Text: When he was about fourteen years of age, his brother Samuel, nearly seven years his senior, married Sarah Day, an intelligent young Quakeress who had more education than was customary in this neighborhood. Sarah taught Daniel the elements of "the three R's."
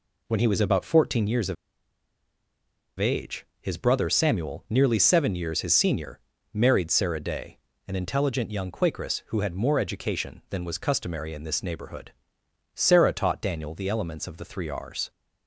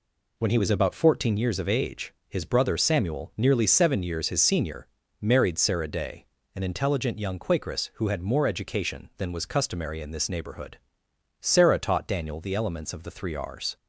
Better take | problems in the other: second | pauses between "of" and "age"; strong; at 1.5 s; 1.4 s long

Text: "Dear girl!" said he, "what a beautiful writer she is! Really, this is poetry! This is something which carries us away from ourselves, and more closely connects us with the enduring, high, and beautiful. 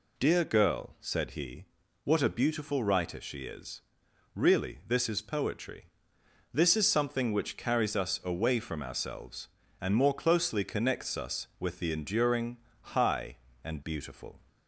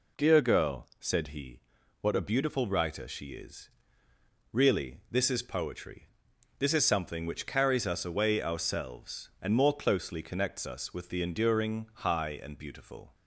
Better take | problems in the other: first | skips "from"; at 8.4 s

